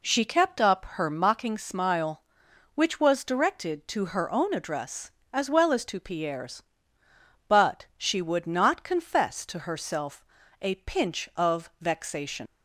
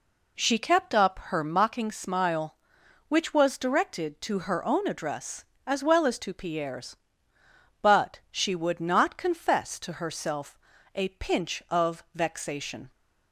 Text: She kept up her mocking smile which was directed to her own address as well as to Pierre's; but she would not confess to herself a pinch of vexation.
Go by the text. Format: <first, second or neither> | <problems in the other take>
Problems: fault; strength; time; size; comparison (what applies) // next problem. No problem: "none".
second | pauses between "herself" and "a"; slight; at 10.2 s; 0.36 s long; slight in the second // leaves "vexation" unfinished; at 12.4 s; 110 ms